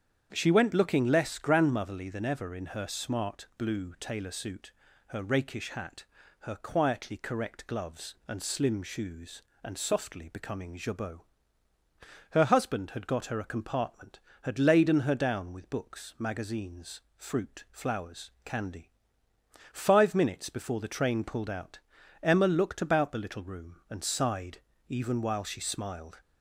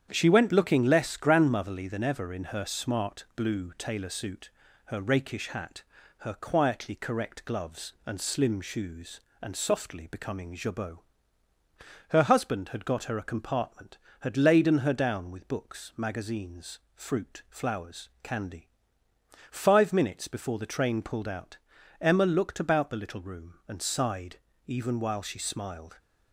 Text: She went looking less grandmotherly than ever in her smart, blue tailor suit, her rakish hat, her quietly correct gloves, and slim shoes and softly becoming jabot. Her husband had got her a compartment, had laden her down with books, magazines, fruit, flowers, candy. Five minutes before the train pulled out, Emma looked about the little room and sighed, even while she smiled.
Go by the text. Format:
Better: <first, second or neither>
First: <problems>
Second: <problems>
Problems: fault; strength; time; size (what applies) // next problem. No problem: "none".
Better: first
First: starts louder than the rest; strong; until 1.3 s; 8.5 dB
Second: gets quieter; noticeable; throughout; 4.5 dB // starts louder than the rest; strong; until 1.1 s; 9 dB